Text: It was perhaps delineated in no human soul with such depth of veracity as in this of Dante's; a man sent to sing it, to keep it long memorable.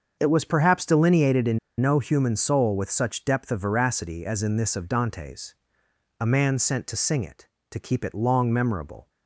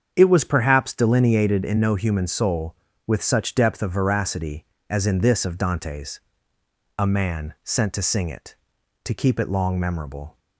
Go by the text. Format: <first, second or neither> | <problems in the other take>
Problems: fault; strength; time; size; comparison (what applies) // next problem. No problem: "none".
second | starts louder than the rest; until 1.2 s; 6.5 dB; strong in the second // pauses between "in" and "no"; slight; at 1.5 s; 0.21 s long